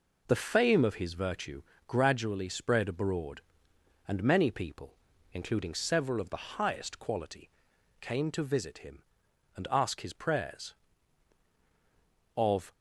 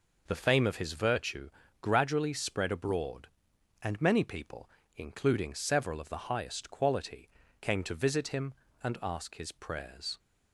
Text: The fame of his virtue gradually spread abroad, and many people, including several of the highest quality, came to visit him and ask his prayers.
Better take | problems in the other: second | pauses between "virtue" and "gradually"; slight; at 1.6 s; 0.26 s long; slight in the second // goes on to say "Of"; slight; from 12.3 s on; 0.36 s long

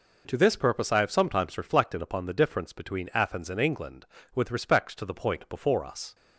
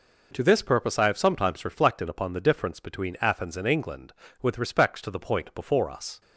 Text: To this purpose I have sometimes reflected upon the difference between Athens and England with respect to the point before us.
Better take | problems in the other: neither | none

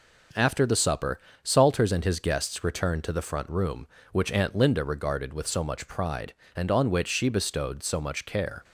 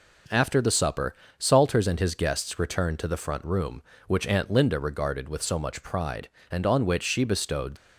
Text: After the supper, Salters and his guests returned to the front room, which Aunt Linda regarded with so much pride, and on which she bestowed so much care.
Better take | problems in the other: first | stops before "so much care"; at 7.7 s

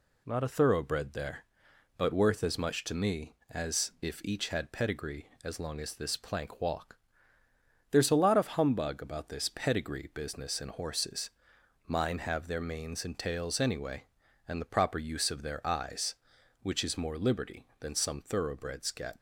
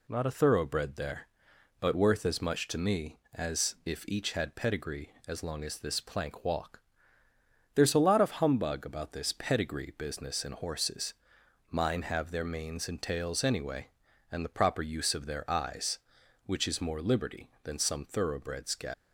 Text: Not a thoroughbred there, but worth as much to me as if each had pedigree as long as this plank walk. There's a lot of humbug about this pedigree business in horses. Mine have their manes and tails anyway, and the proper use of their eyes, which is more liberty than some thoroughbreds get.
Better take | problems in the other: first | leaves "get" unfinished; at 18.9 s; 80 ms

